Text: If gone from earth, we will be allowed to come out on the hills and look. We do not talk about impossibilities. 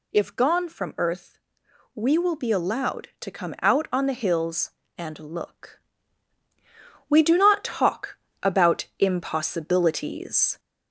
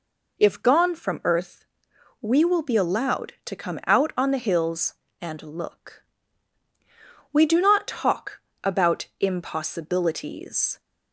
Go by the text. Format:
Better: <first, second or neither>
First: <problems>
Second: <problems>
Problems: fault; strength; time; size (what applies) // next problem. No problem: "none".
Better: second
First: gets louder; slight; throughout; 3 dB // pauses between "talk" and "about"; slight; at 8.1 s; 0.26 s long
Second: pauses between "talk" and "about"; slight; at 8.3 s; 0.24 s long